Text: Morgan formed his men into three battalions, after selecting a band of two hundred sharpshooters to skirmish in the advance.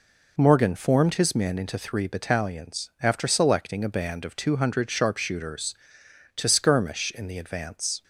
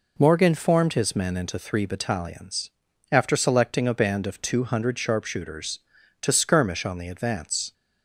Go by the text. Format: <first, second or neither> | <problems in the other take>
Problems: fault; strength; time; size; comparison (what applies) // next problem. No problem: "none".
first | says "on" for "in"; at 6.8 s